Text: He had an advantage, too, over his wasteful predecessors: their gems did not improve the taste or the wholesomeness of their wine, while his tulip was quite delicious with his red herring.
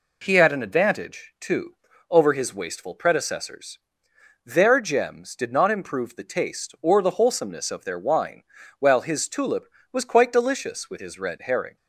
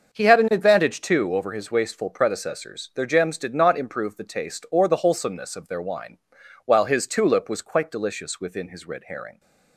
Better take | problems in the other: first | starts louder than the rest; until 1.1 s; 6.5 dB // says "within" for "with"; at 8.3 s

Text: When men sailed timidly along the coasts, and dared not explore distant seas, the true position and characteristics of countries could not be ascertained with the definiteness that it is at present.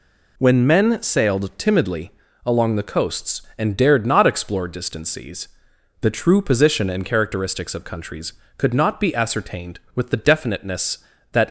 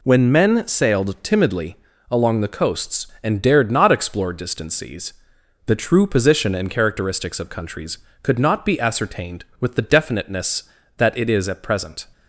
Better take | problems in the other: second | pauses between "timidly" and "along"; slight; at 2.1 s; 0.34 s long; slight in the second // stops before "it is at present"; at 11.4 s

